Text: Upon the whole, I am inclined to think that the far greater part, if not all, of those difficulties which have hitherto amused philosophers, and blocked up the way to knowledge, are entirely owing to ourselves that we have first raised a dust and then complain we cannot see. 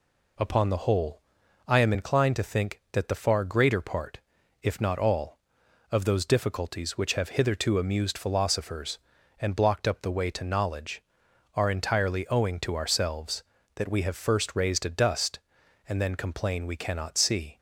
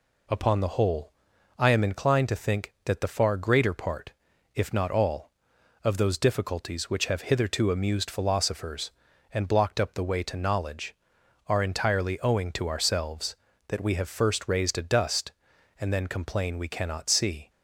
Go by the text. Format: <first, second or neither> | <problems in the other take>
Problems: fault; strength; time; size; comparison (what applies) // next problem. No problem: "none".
neither | none